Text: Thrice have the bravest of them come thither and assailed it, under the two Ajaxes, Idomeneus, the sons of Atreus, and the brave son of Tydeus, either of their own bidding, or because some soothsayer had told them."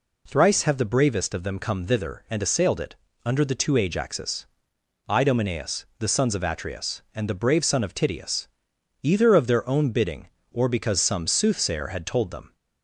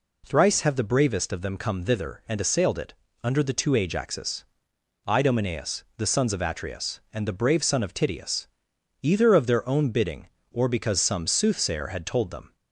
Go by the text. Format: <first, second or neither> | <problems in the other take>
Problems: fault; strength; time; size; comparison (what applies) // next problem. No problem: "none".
neither | none